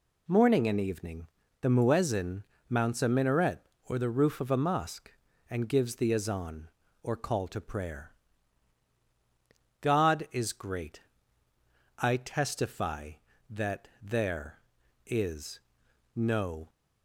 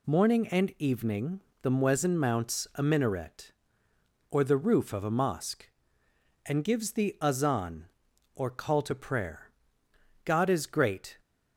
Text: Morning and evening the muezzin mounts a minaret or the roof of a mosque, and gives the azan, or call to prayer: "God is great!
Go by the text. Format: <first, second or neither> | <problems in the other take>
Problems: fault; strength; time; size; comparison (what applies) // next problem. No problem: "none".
second | pauses between "evening" and "the"; slight; at 1.2 s; 0.36 s long; slight in the second // pauses between "muezzin" and "mounts"; slight; at 2.4 s; 0.24 s long // goes on to say "I testify that there is no"; strong; from 11.9 s on; 4.7 s long